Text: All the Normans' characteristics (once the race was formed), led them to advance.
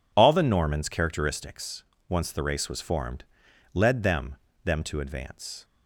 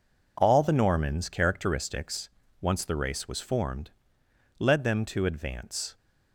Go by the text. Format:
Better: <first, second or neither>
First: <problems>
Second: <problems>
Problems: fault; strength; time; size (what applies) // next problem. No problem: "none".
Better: second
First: says "them" twice; at 4.6 s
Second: none